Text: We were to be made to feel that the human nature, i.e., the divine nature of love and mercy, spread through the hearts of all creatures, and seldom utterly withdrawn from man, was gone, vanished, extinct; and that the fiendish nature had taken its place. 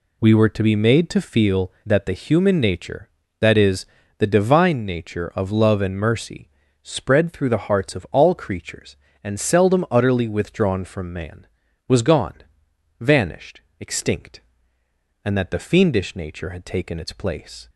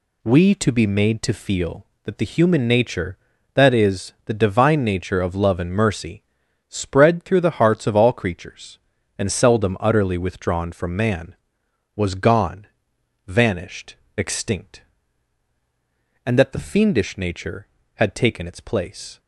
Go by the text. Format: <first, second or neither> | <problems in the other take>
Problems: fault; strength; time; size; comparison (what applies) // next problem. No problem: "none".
first | skips "were"; at 0.5 s